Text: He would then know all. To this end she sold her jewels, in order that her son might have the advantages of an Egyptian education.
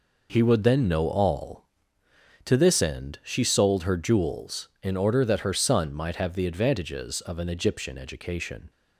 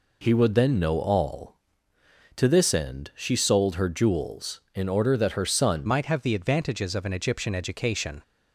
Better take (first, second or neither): first